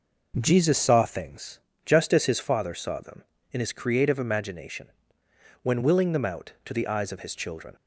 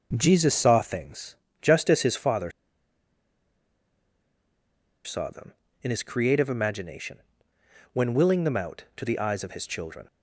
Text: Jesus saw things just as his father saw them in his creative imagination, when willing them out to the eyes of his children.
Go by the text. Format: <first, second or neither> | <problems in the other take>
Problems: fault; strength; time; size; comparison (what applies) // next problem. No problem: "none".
first | pauses between "things" and "just"; slight; at 1.3 s; 0.24 s long; slight in the first // pauses between "father" and "saw"; strong; at 2.4 s; 2.5 s long